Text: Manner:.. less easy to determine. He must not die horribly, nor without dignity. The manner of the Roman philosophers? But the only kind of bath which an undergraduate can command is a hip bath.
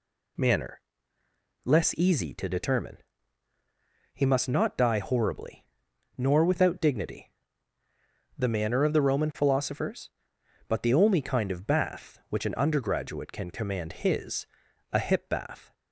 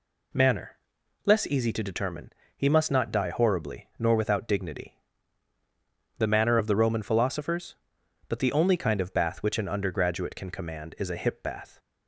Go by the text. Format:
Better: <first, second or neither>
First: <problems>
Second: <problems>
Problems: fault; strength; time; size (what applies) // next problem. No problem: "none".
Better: second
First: says "his" for "is"; at 13.9 s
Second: none